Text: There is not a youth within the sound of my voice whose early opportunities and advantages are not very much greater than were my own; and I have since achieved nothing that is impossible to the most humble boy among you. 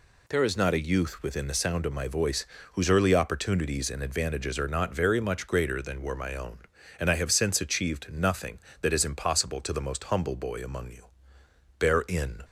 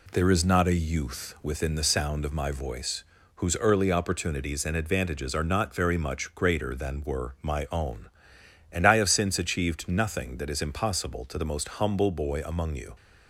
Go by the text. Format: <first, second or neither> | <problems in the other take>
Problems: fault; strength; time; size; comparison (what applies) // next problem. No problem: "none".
second | pauses between "voice" and "whose"; slight; at 2.4 s; 0.26 s long; slight in the second // goes on to say "Bear in"; noticeable; from 11.7 s on; 0.66 s long